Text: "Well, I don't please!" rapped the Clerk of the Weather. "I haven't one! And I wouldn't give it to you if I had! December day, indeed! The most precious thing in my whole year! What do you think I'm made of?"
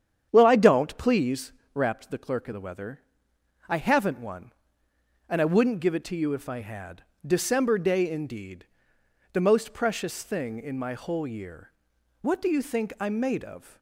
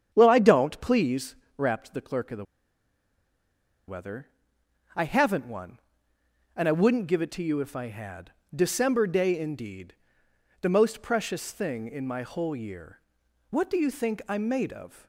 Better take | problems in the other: first | starts louder than the rest; strong; until 1.1 s; 8.5 dB; strong in the first // pauses between "the" and "Weather"; strong; at 2.4 s; 1.4 s long

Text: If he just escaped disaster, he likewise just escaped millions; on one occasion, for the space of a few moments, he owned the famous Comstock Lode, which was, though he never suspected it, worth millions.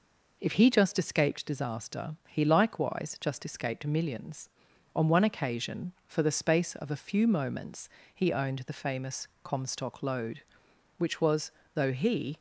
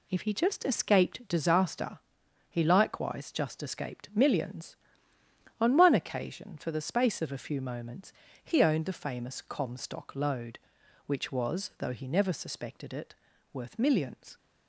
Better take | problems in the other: second | pauses between "famous" and "Comstock"; slight; at 9.2 s; 0.16 s long // stops before "never suspected it worth millions"; at 12.3 s

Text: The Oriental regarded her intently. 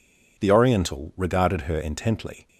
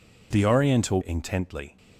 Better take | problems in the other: first | skips "regarded her"; at 1.0 s

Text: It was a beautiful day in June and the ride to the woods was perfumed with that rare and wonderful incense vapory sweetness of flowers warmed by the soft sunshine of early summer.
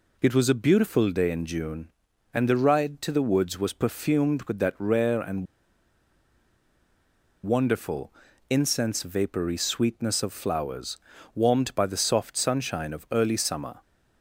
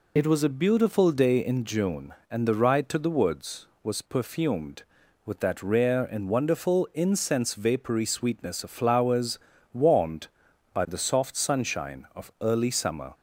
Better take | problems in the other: second | pauses between "and" and "wonderful"; strong; at 5.4 s; 1.9 s long // pauses between "wonderful" and "incense"; slight; at 8.1 s; 0.36 s long // pauses between "flowers" and "warmed"; at 10.9 s; 0.38 s long; also in the second

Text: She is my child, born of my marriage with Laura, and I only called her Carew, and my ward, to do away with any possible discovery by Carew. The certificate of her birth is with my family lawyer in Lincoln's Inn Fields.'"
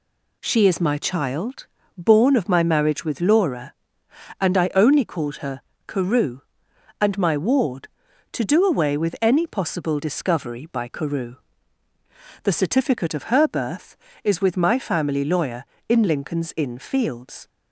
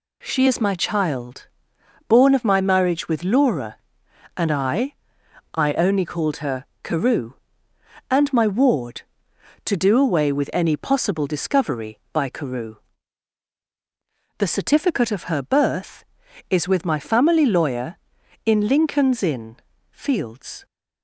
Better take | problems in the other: first | says "I" twice; at 5.5 s // pauses between "her" and "Carew"; slight; at 6.6 s; 0.18 s long; slight in the first // pauses between "Inn" and "Fields"; slight; at 19.5 s; 0.34 s long

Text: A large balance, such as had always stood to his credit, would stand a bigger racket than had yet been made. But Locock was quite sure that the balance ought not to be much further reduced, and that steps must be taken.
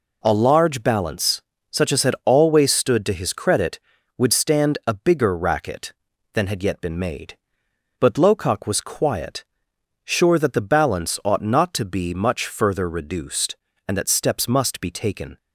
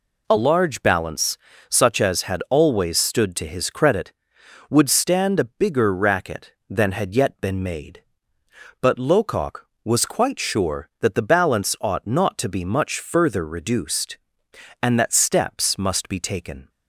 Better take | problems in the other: second | says "quiet" for "quite"; at 8.8 s

